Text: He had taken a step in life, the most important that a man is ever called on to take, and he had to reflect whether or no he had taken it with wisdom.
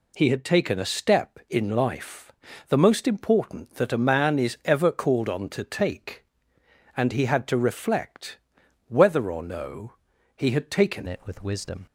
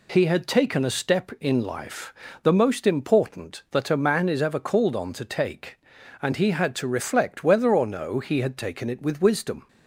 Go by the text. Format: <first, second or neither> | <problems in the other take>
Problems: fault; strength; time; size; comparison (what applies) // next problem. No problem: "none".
second | pauses between "reflect" and "whether"; noticeable; at 8.3 s; 0.48 s long // pauses between "no" and "he"; at 9.9 s; 0.44 s long // changes voice at "it"; from 11.0 s on; 0.8 s long